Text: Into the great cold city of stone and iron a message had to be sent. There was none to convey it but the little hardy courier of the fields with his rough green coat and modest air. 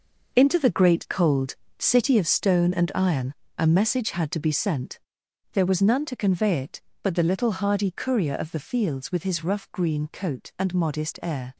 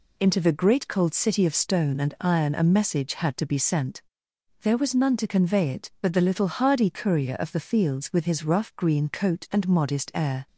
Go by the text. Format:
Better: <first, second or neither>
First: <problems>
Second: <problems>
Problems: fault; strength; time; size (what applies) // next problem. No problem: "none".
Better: second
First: gets quieter; strong; throughout; 9 dB // pauses between "cold" and "city"; slight; at 1.5 s; 0.24 s long // pauses between "iron" and "a"; slight; at 3.3 s; 0.24 s long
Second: none